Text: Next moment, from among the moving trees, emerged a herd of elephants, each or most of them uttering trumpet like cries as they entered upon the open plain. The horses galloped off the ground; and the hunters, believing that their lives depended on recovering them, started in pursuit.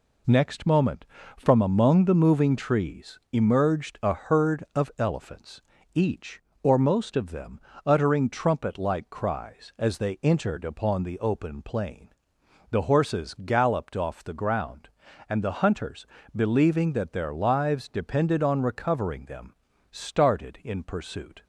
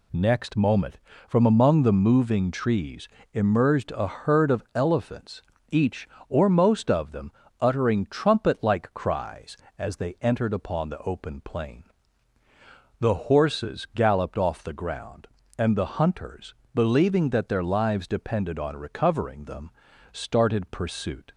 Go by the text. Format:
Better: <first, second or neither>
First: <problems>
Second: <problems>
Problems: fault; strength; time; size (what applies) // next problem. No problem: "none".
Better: first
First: pauses between "them" and "uttering"; slight; at 7.5 s; 0.26 s long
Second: pauses between "them" and "uttering"; slight; at 7.3 s; 0.30 s long // skips "in"; at 20.7 s